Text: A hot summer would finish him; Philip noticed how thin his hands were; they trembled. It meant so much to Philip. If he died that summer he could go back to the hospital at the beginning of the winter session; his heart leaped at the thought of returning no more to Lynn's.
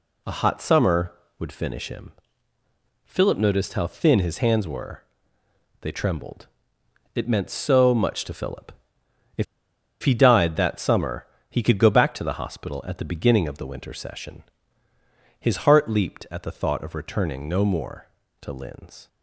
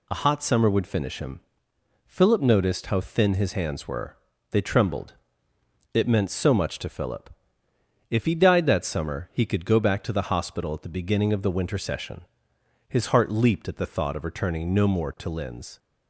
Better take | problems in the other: second | pauses between "If" and "he"; noticeable; at 9.4 s; 0.58 s long // pauses between "summer" and "he"; slight; at 11.2 s; 0.24 s long

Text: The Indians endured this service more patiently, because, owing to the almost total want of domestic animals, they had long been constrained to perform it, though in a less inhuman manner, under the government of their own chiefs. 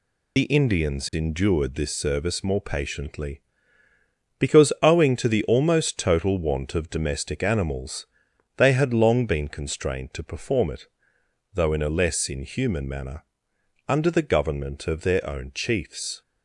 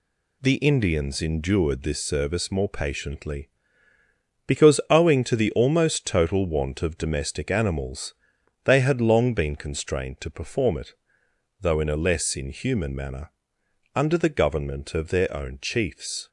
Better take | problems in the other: second | loses the start of "The"; at 0.3 s; 70 ms

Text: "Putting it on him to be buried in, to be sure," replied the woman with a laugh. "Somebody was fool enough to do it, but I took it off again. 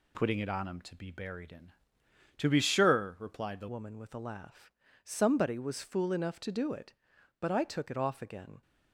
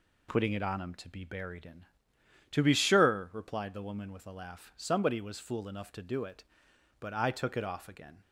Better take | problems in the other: second | changes voice at "woman"; from 3.6 s on; 5.0 s long

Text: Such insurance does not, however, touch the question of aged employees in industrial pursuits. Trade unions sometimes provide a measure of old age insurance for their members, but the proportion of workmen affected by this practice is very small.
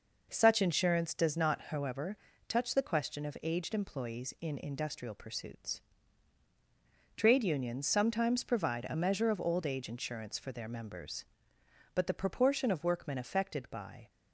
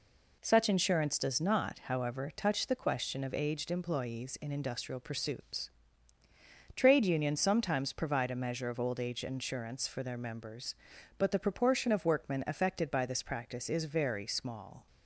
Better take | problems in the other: second | stops before "this practice is very small"; at 14.0 s

